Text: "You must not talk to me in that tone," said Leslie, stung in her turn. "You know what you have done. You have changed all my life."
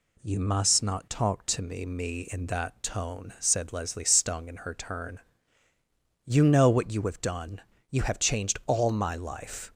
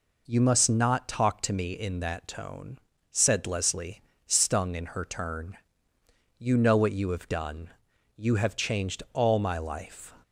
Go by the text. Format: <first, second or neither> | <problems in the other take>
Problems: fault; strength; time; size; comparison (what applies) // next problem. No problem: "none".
second | says "me" twice; at 1.8 s